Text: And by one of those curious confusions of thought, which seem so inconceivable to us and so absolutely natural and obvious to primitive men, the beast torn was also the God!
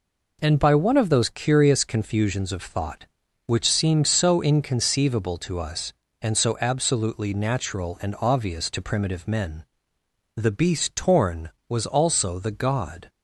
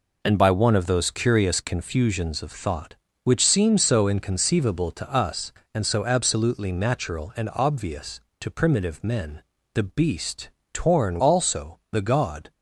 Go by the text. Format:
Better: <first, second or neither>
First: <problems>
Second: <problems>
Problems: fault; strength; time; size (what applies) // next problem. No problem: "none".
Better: first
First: none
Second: pauses between "beast" and "torn"; slight; at 10.4 s; 0.24 s long // skips "was"; at 11.1 s